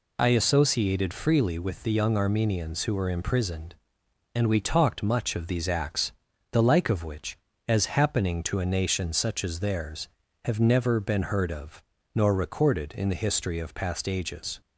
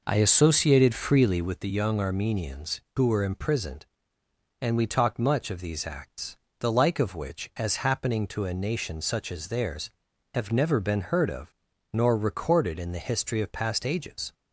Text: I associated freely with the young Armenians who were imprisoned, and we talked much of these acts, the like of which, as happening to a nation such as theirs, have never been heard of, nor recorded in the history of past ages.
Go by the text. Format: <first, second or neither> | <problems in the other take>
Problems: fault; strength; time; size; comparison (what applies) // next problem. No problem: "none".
first | starts louder than the rest; noticeable; until 1.6 s; 5 dB